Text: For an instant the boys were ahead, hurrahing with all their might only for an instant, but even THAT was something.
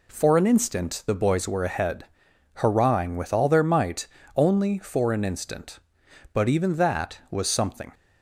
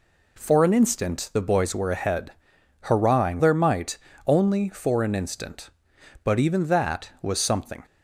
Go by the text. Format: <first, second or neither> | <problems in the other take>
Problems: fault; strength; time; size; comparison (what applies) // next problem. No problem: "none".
first | skips "with all"; at 3.4 s // pauses between "might" and "only"; slight; at 3.9 s; 0.26 s long; slight in the first